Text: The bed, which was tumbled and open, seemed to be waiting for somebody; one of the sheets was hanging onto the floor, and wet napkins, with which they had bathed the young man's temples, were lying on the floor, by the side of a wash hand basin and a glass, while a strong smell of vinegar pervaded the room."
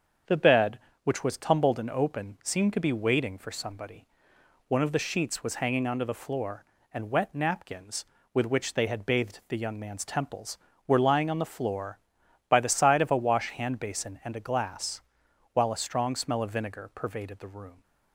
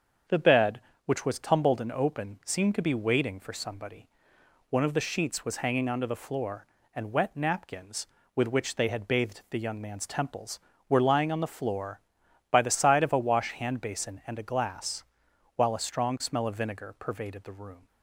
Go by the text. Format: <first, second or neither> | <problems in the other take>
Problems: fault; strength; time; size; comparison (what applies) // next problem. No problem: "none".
neither | starts louder than the rest; the same in both